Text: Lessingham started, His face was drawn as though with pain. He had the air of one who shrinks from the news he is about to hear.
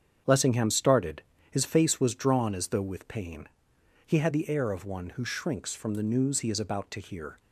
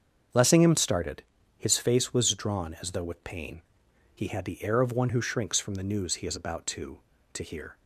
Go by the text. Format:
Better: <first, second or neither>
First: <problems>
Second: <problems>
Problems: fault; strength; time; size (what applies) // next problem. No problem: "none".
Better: first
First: starts louder than the rest; strong; until 1.5 s; 7.5 dB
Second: starts louder than the rest; until 1.6 s; 7 dB // says "to" twice; at 7.3 s